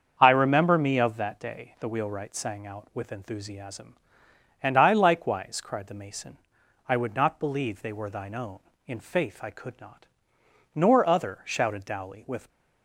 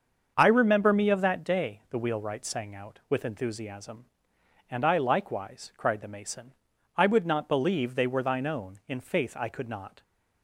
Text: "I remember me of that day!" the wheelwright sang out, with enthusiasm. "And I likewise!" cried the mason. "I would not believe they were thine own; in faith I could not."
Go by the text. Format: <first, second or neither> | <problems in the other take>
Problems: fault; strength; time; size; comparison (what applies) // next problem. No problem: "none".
second | starts louder than the rest; until 1.2 s; 7 dB; also in the second // goes on to say "Nor other shouted Dowley with"; strong; from 10.7 s on; 1.7 s long